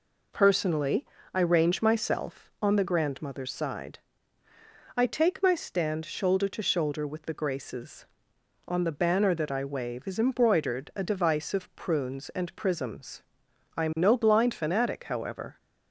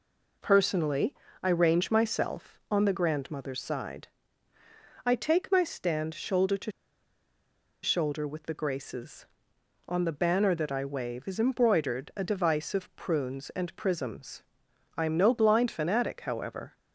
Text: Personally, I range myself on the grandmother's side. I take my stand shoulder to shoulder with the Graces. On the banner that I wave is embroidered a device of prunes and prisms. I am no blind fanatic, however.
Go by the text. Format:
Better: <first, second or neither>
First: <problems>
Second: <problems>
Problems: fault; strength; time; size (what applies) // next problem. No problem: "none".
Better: first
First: none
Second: pauses between "to" and "shoulder"; at 6.7 s; 1.1 s long